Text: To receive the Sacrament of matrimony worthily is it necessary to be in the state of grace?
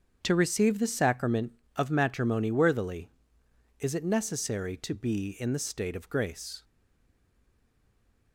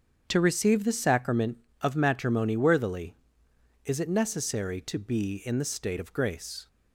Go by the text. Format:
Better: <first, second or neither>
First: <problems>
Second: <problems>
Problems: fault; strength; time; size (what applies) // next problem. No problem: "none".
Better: second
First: starts louder than the rest; until 1.2 s; 7 dB // stays silent after the last word; noticeable; from 6.6 s on; 1.7 s long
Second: starts louder than the rest; strong; until 1.2 s; 7.5 dB